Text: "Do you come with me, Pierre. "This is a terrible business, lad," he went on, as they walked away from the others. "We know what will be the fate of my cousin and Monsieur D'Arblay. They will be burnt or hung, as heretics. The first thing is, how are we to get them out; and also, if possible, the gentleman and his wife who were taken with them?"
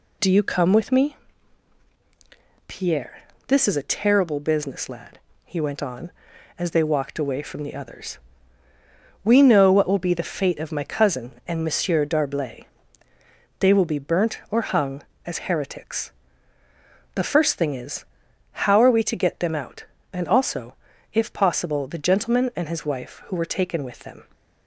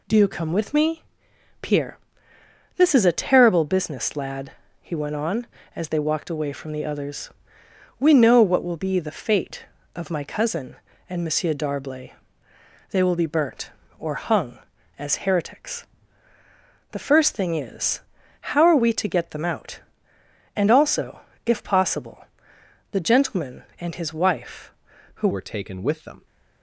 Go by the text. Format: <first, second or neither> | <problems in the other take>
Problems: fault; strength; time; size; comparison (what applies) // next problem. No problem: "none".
first | changes voice at "were"; from 25.3 s on; 0.9 s long